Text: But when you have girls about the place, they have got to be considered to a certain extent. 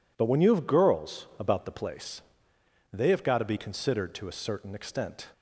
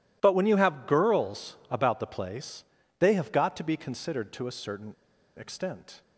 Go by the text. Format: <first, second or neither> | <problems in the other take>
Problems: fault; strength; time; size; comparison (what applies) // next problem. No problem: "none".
first | pauses between "certain" and "extent"; at 4.9 s; 0.44 s long